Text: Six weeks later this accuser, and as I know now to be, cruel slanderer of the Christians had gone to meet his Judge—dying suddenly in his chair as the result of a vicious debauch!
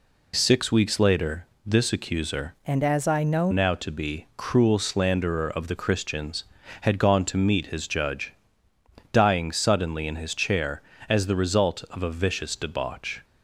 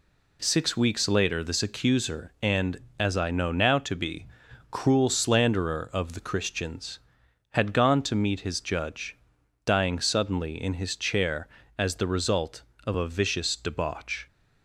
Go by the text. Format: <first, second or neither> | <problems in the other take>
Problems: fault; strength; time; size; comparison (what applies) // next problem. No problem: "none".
second | pauses between "later" and "this"; slight; at 1.4 s; 0.18 s long // changes voice from "and" to "know"; from 2.6 to 3.5 s; 0.9 s long